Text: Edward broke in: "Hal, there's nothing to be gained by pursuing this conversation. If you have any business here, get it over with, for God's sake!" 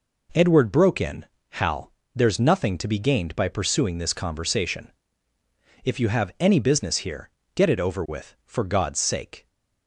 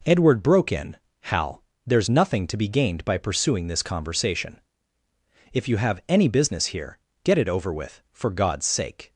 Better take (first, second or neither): neither